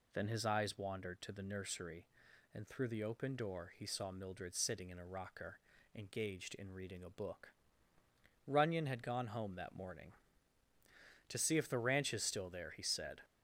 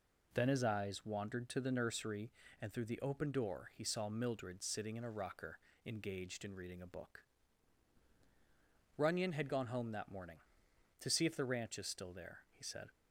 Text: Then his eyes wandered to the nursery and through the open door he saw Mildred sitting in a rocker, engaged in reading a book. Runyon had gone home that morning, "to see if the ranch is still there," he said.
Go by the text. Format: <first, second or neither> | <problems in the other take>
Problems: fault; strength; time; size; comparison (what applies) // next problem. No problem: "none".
neither | none